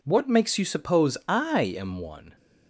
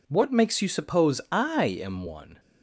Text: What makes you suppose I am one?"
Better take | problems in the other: neither | none

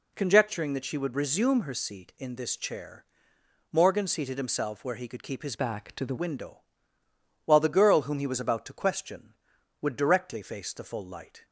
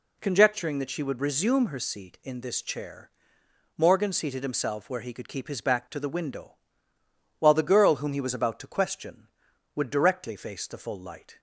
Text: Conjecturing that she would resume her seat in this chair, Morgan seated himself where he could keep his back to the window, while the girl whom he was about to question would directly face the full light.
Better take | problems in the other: second | changes voice from "back" to "the"; from 5.5 to 6.1 s; 0.6 s long

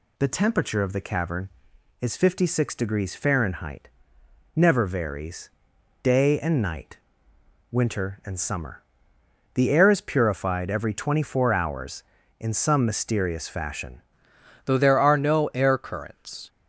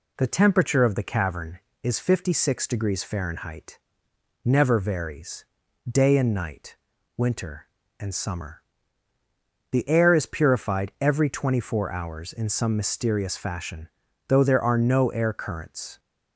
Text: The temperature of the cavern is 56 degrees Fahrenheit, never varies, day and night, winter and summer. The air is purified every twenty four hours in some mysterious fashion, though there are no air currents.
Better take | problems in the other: second | changes voice at "though"; from 14.6 s on; 1.8 s long

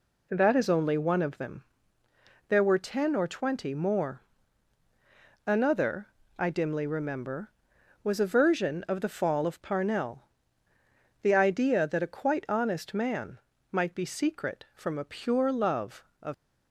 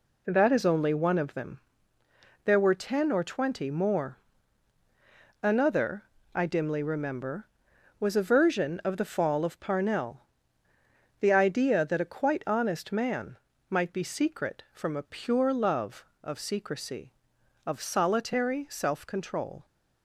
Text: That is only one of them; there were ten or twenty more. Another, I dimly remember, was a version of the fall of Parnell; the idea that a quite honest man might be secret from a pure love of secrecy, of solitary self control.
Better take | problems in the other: second | pauses between "man" and "might"; slight; at 13.3 s; 0.34 s long; slight in the second // stops before "secrecy of solitary self control"; at 16.3 s

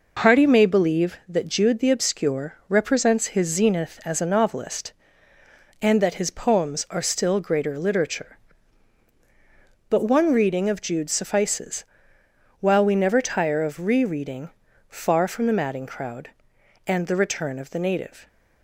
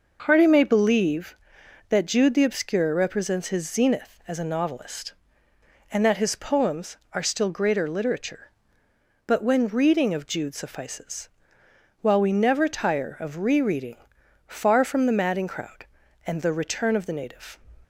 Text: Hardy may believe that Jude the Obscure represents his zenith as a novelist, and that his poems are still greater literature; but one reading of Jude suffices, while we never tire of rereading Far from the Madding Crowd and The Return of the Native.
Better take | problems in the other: first | says "when" for "one"; at 9.4 s // pauses between "rereading" and "Far"; noticeable; at 13.9 s; 0.50 s long; also in the first

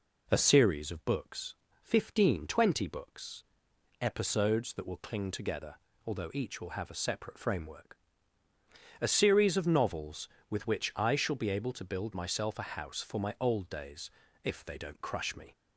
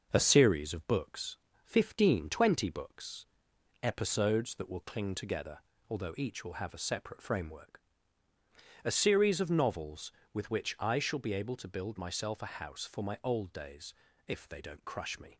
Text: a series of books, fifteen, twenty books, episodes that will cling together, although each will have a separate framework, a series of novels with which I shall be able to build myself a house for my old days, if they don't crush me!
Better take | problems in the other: first | gets quieter; throughout; 3.5 dB

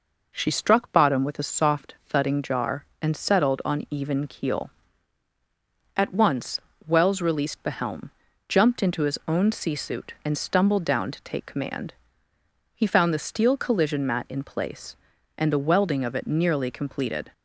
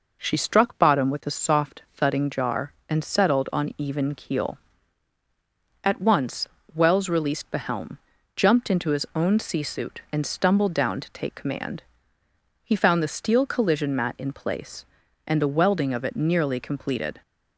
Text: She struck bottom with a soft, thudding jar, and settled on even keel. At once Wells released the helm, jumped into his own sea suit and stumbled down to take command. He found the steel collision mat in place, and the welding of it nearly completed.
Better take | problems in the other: neither | pauses between "once" and "Wells"; slight; the same in both

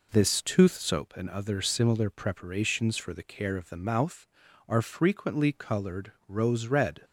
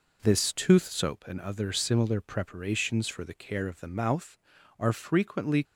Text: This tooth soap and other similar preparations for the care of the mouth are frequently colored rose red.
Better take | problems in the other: first | stops before "colored rose red"; at 5.6 s

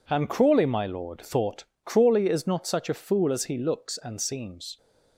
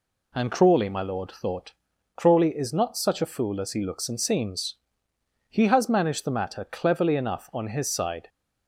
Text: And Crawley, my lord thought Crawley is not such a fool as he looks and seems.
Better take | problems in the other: first | pauses between "thought" and "Crawley"; at 1.7 s; 0.44 s long; slight in the first // goes on to say "He has managed the matter cleverly enough on his side"; strong; from 5.4 s on; 2.8 s long

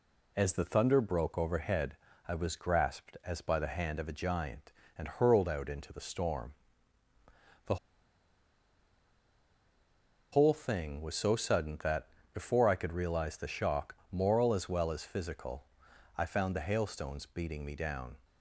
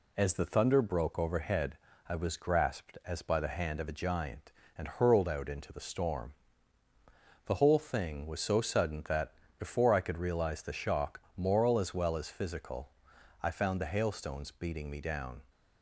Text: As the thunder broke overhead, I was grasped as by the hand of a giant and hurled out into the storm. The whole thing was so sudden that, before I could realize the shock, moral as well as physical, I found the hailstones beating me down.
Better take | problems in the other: second | pauses between "The" and "whole"; strong; at 7.7 s; 2.5 s long

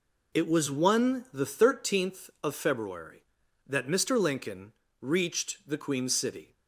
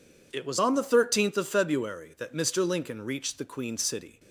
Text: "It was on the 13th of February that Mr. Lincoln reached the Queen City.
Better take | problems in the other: second | says "one" for "on"; at 0.7 s // pauses between "Lincoln" and "reached"; slight; at 4.7 s; 0.30 s long

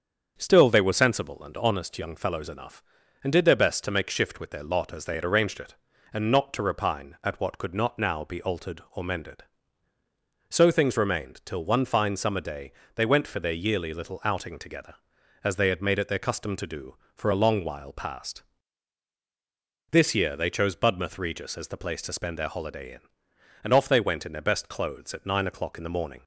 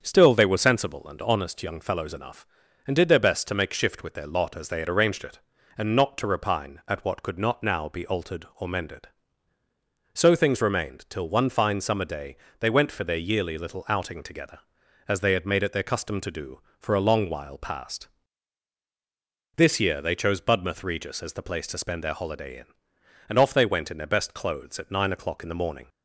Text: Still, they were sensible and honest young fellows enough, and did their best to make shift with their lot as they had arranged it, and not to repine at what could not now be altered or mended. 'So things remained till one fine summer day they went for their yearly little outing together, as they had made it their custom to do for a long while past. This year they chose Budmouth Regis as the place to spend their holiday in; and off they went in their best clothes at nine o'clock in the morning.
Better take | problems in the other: neither | starts louder than the rest; strong; the same in both // pauses between "day" and "they"; slight; the same in both

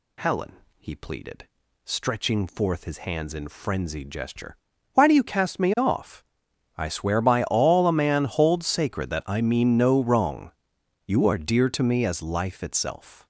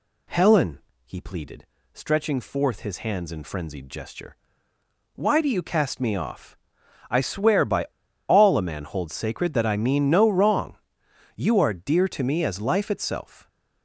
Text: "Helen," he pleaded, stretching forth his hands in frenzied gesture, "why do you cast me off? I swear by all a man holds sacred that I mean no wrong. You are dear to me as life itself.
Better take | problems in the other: first | pauses between "by" and "all"; at 7.8 s; 0.41 s long

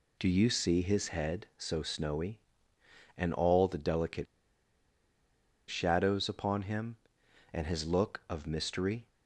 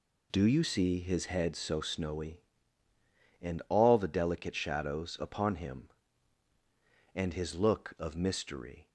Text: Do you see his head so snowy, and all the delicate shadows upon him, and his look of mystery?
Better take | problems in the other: second | pauses between "delicate" and "shadows"; strong; at 4.2 s; 1.4 s long

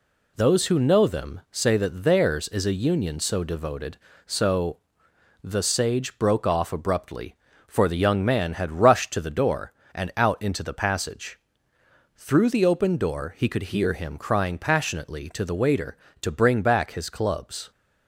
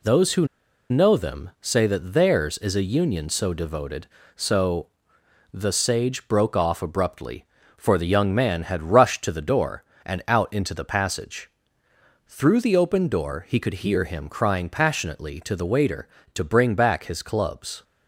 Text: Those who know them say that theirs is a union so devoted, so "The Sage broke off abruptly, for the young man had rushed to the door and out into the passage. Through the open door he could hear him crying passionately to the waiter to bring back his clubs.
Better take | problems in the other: first | pauses between "who" and "know"; at 0.4 s; 0.43 s long // pauses between "so" and "The"; noticeable; at 4.8 s; 0.66 s long; noticeable in the first

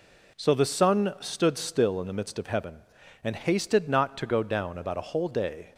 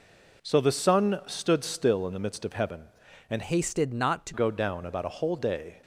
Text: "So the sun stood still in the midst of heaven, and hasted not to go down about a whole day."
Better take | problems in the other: first | changes voice from "hasted" to "to"; from 3.4 to 4.3 s; 0.9 s long

